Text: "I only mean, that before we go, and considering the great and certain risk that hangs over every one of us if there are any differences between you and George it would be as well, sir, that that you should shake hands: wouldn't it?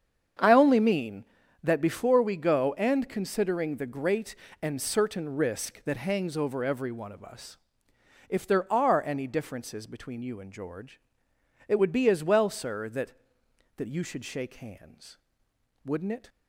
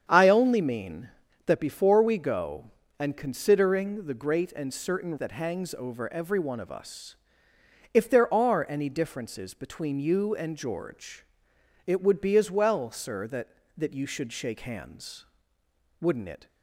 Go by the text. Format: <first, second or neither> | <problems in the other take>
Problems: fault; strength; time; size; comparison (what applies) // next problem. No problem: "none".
first | starts louder than the rest; strong; until 1.1 s; 8 dB; strong in the first // skips "risk"; at 5.1 s // pauses between "us" and "if"; noticeable; at 7.1 s; 0.78 s long; noticeable in the first // pauses between "George" and "it"; noticeable; at 11.2 s; 0.62 s long; noticeable in the first